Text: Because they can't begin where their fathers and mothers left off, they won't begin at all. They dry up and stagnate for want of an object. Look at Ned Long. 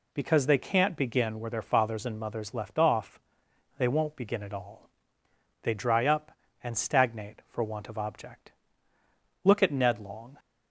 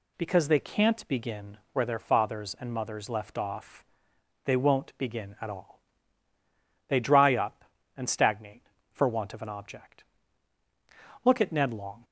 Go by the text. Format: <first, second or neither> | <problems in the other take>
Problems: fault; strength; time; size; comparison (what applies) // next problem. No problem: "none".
second | skips "an"; at 7.9 s